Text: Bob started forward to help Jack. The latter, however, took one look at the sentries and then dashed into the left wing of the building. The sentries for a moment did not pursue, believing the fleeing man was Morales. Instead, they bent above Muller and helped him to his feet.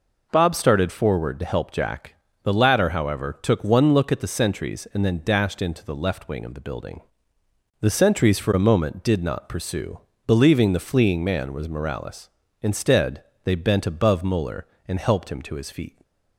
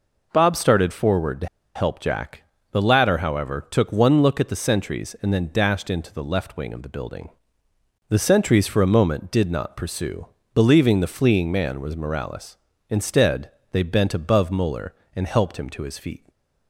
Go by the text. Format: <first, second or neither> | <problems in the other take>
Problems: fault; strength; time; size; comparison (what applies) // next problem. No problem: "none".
first | pauses between "to" and "help"; slight; at 1.4 s; 0.27 s long